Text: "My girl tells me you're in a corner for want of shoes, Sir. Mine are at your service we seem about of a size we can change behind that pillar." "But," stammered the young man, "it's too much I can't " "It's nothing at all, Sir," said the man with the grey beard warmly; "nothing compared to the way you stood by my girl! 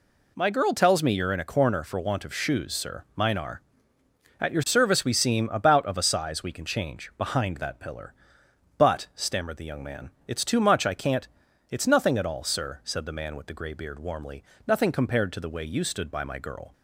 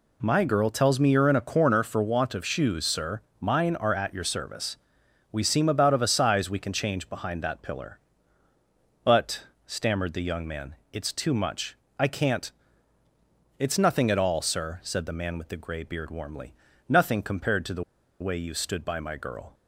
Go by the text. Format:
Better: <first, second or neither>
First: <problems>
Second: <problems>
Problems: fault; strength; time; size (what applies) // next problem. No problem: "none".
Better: first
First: none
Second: pauses between "service" and "we"; noticeable; at 4.7 s; 0.54 s long // pauses between "much" and "I"; slight; at 11.7 s; 0.22 s long // pauses between "the" and "way"; at 17.8 s; 0.39 s long